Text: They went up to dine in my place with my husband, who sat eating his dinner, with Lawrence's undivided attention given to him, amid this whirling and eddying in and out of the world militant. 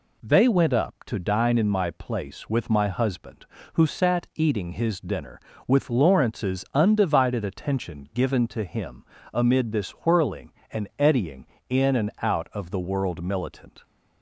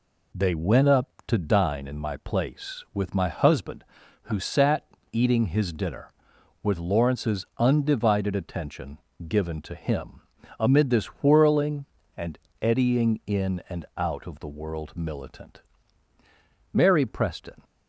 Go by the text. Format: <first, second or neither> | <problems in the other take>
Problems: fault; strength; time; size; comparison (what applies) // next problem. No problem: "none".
first | pauses between "sat" and "eating"; slight; at 4.8 s; 0.26 s long // pauses between "attention" and "given"; slight; at 8.9 s; 0.30 s long // pauses between "this" and "whirling"; slight; at 11.0 s; 0.16 s long // pauses between "and" and "eddying"; slight; at 12.3 s; 0.24 s long // goes on to say "Mary Preston"; noticeable; from 16.7 s on; 0.92 s long